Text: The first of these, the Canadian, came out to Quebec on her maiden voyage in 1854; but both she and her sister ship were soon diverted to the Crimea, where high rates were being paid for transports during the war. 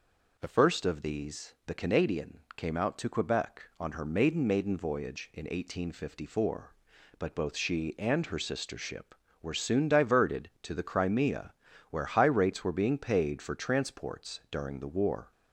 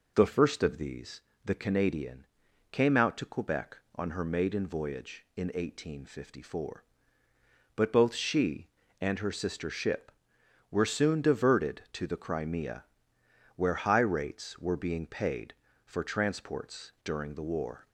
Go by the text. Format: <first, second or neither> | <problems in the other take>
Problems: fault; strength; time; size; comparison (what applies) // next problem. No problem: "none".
second | says "maiden" twice; at 4.4 s